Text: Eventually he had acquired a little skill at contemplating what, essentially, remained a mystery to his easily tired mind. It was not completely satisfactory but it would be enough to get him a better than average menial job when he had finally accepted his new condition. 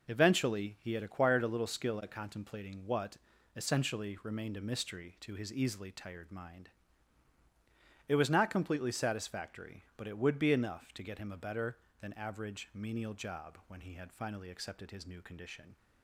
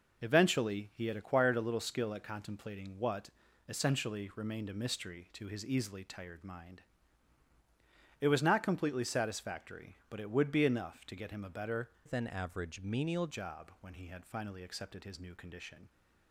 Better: first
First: none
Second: changes voice from "than" to "menial"; from 12.0 to 13.2 s; 1.2 s long

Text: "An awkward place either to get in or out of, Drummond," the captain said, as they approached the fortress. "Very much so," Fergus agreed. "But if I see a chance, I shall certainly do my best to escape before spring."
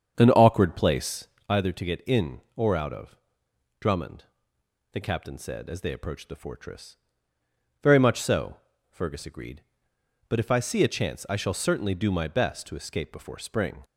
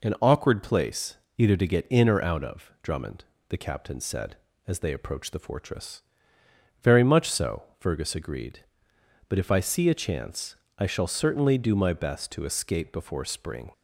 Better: second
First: starts louder than the rest; strong; until 1.6 s; 7.5 dB // pauses between "place" and "either"; slight; at 1.2 s; 0.22 s long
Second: pauses between "place" and "either"; slight; at 1.1 s; 0.20 s long

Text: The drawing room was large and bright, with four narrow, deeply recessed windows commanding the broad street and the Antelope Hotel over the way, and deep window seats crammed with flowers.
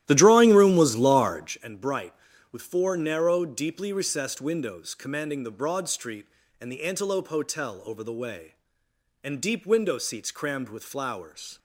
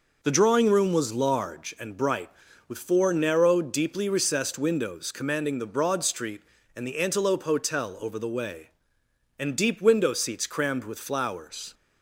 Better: second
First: starts louder than the rest; strong; until 1.6 s; 13 dB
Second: none

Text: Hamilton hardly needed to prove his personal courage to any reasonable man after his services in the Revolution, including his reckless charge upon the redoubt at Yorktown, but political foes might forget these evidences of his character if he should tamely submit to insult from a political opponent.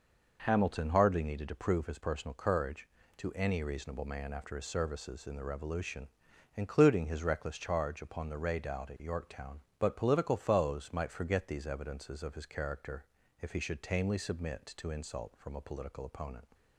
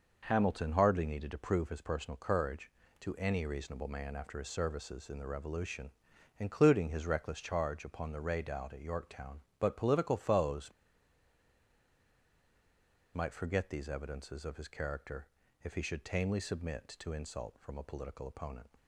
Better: first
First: pauses between "character" and "if"; slight; at 13.0 s; 0.34 s long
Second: pauses between "foes" and "might"; strong; at 10.6 s; 2.4 s long // pauses between "character" and "if"; slight; at 15.2 s; 0.34 s long

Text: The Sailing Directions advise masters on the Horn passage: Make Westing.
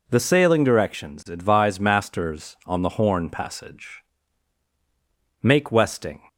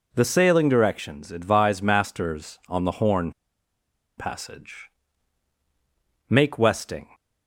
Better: first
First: none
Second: pauses between "Horn" and "passage"; noticeable; at 3.3 s; 0.86 s long

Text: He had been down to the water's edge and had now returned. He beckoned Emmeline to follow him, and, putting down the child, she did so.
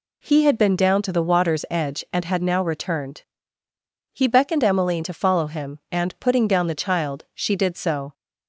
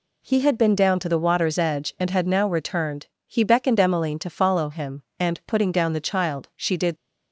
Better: first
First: none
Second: stops before "so"; at 6.9 s

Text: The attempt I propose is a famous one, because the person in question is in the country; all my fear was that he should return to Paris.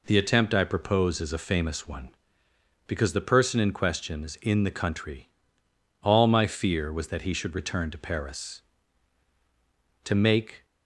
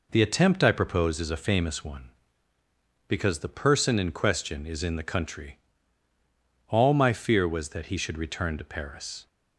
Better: second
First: goes on to say "To make"; noticeable; from 10.0 s on; 0.62 s long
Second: none

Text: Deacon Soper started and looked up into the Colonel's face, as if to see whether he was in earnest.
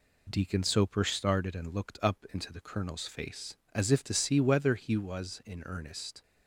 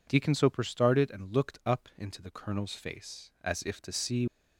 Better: first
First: none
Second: stops before "whether he was in earnest"; at 4.2 s

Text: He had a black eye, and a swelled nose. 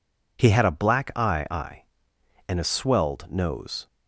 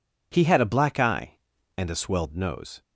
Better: second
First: says "eye" twice; at 1.5 s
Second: none

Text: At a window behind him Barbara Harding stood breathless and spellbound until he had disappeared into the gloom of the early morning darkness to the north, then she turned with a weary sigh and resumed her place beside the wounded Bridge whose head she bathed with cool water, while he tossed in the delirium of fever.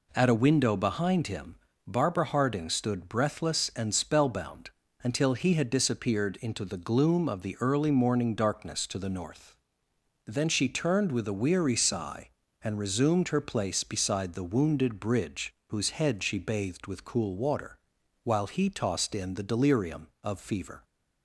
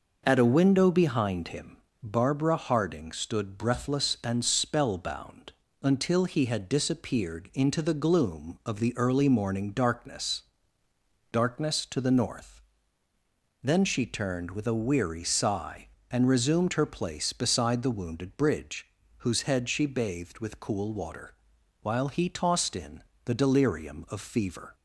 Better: first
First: pauses between "him" and "Barbara"; slight; at 1.5 s; 0.30 s long // pauses between "spellbound" and "until"; slight; at 4.7 s; 0.32 s long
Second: pauses between "him" and "Barbara"; slight; at 1.7 s; 0.26 s long // pauses between "spellbound" and "until"; slight; at 5.5 s; 0.30 s long // says "darkness" twice; at 11.3 s // pauses between "Bridge" and "whose"; slight; at 18.8 s; 0.32 s long // pauses between "in" and "the"; slight; at 23.0 s; 0.24 s long

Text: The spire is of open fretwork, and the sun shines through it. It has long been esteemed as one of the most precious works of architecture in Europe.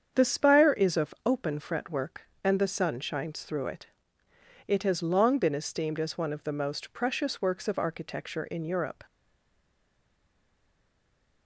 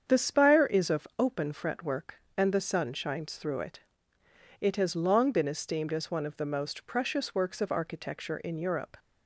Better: second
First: starts louder than the rest; strong; until 1.2 s; 7.5 dB // stays silent after the last word; from 9.0 s on; 2.4 s long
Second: starts louder than the rest; strong; until 1.2 s; 7.5 dB

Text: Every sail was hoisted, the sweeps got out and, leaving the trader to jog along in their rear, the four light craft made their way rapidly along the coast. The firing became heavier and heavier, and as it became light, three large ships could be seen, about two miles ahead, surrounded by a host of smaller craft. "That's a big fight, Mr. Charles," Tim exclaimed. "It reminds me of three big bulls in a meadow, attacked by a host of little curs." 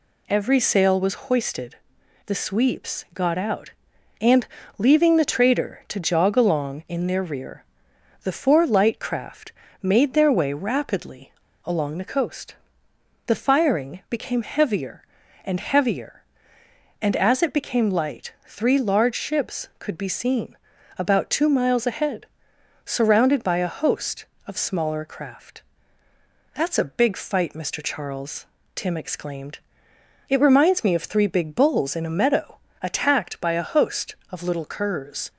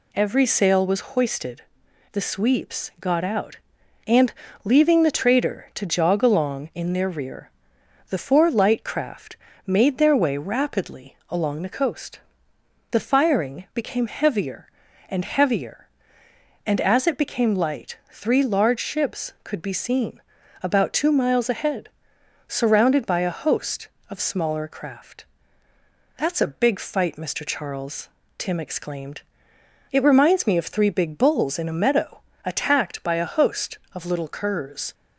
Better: second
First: pauses between "craft" and "made"; slight; at 9.5 s; 0.32 s long // pauses between "rapidly" and "along"; slight; at 11.3 s; 0.31 s long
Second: pauses between "craft" and "made"; slight; at 9.3 s; 0.32 s long

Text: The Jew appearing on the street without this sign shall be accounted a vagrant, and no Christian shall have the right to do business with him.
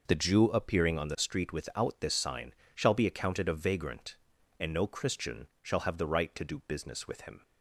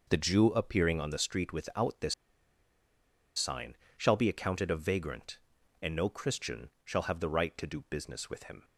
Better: first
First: pauses between "sign" and "shall"; slight; at 2.5 s; 0.20 s long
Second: pauses between "this" and "sign"; at 2.1 s; 1.2 s long // pauses between "sign" and "shall"; slight; at 3.7 s; 0.20 s long

